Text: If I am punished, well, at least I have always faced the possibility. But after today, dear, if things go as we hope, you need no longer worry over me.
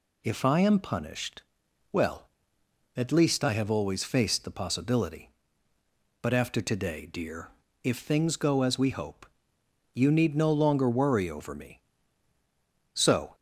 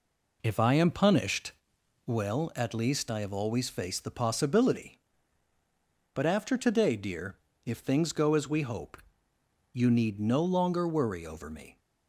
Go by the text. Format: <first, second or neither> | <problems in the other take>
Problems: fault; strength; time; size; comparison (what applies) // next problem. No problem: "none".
second | goes on to say "So"; slight; from 12.9 s on; 0.42 s long